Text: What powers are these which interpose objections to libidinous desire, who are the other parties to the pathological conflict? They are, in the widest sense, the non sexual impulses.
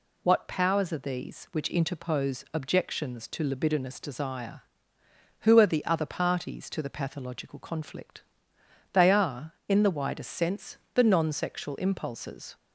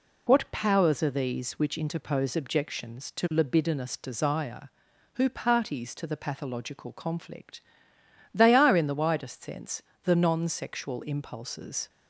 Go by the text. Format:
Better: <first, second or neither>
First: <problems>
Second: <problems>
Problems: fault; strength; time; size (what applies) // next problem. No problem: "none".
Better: first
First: none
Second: skips "are the other"; at 5.2 s